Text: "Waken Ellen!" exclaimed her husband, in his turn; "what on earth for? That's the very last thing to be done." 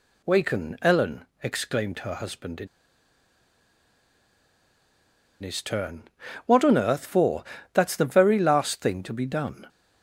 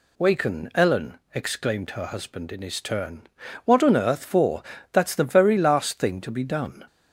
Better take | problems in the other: second | pauses between "in" and "his"; strong; at 2.6 s; 2.7 s long

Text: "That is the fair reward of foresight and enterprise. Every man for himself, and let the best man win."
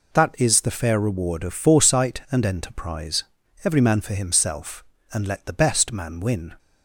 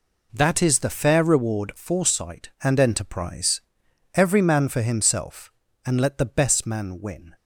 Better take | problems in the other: first | skips "of"; at 1.7 s

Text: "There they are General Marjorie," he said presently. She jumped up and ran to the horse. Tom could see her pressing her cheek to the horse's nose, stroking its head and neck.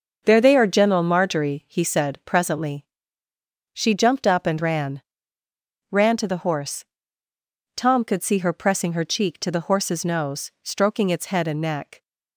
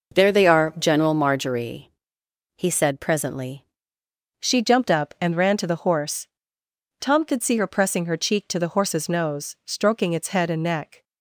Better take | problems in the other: second | starts louder than the rest; noticeable; until 1.2 s; 6 dB // says "ran" twice; at 5.8 s

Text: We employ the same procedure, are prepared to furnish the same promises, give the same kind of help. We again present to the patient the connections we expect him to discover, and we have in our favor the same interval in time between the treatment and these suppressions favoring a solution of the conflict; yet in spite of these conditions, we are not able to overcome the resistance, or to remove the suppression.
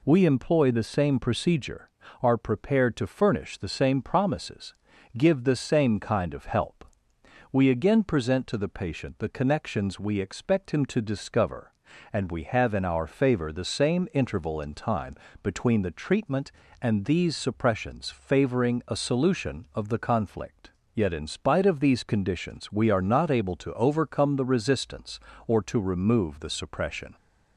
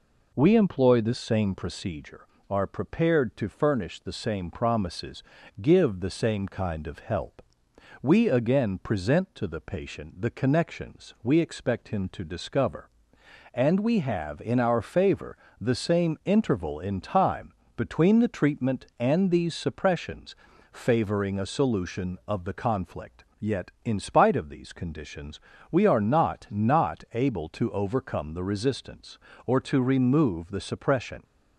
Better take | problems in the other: first | pauses between "favor" and "the"; slight; at 15.3 s; 0.24 s long // pauses between "time" and "between"; slight; at 17.5 s; 0.24 s long; slight in the first // pauses between "suppressions" and "favoring"; at 20.3 s; 0.38 s long // says "not" twice; at 26.4 s

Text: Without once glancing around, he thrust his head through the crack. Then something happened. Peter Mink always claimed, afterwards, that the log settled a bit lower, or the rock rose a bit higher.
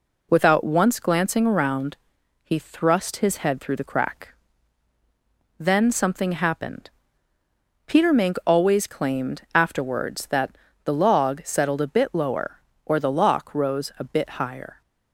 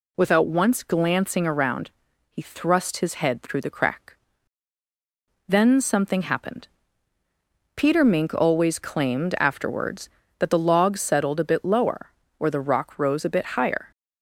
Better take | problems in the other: second | pauses between "that" and "the"; slight; at 10.5 s; 0.34 s long // says "lock" for "rock"; at 13.1 s

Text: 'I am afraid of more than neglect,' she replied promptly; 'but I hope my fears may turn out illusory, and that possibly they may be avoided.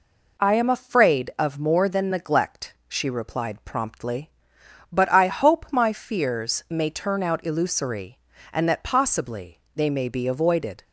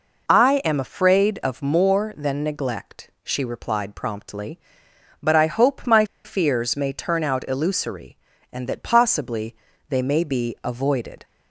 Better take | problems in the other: first | pauses between "my" and "fears"; slight; at 6.0 s; 0.20 s long // pauses between "possibly" and "they"; slight; at 9.5 s; 0.32 s long; slight in the first

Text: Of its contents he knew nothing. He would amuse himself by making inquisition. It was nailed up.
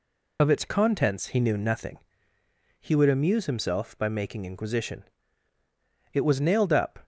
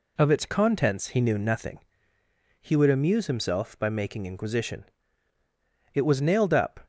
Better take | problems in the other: second | loses the start of "Of"; at 0.3 s; 30 ms

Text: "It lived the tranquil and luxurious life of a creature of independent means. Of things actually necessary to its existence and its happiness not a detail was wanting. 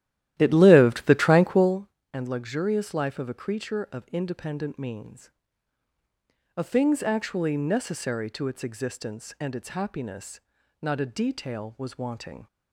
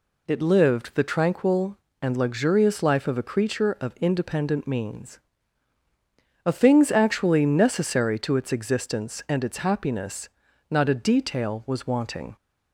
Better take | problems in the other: second | starts louder than the rest; strong; until 1.8 s; 13 dB // pauses between "happiness" and "not"; at 10.4 s; 0.40 s long; also in the second

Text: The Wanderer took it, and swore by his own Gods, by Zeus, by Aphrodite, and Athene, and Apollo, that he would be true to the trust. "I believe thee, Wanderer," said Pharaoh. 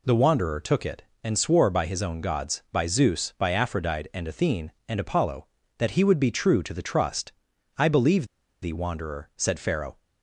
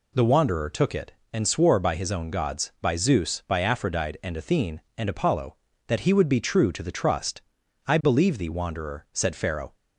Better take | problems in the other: second | pauses between "believe" and "thee"; slight; at 8.2 s; 0.35 s long

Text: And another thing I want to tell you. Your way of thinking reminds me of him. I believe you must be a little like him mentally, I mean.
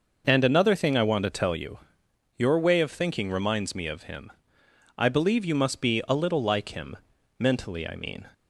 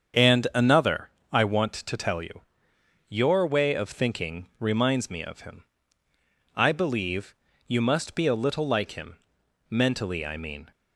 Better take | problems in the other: first | starts louder than the rest; strong; until 1.4 s; 7.5 dB // skips "thing"; at 1.2 s // pauses between "believe" and "you"; slight; at 7.3 s; 0.32 s long // pauses between "him" and "mentally"; noticeable; at 9.1 s; 0.52 s long; also in the first

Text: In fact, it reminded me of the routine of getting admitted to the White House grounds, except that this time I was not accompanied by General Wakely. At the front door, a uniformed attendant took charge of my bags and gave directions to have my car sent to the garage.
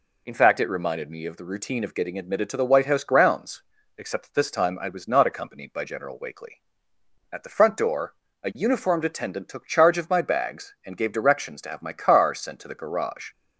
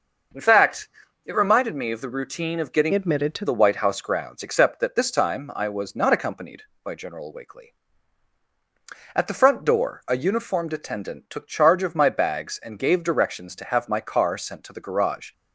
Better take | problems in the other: first | starts louder than the rest; noticeable; until 1.6 s; 6 dB // changes voice from "admitted" to "to"; from 2.9 to 3.4 s; 0.5 s long

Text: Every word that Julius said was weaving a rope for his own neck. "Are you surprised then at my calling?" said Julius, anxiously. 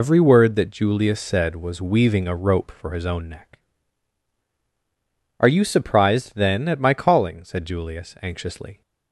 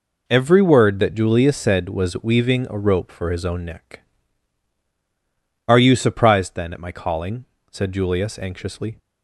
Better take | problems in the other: second | loses the start of "Every"; at 0.0 s; 85 ms

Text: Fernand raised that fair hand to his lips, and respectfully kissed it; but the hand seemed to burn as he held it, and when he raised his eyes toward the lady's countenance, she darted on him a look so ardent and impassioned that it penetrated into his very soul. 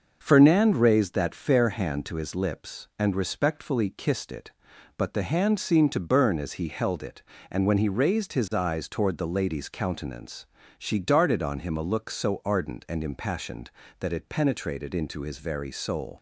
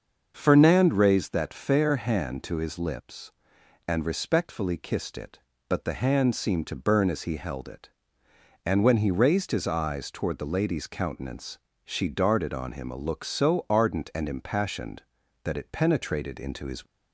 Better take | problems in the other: first | starts louder than the rest; until 1.3 s; 6.5 dB; also in the first // stops before "very soul"; at 16.8 s

